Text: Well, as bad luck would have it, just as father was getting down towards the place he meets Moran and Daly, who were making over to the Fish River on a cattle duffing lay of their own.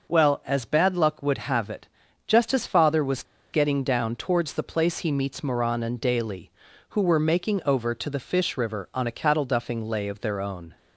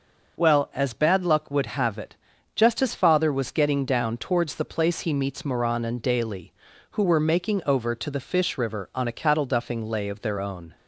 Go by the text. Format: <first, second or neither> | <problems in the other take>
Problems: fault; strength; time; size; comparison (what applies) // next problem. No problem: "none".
second | pauses between "was" and "getting"; slight; at 3.2 s; 0.28 s long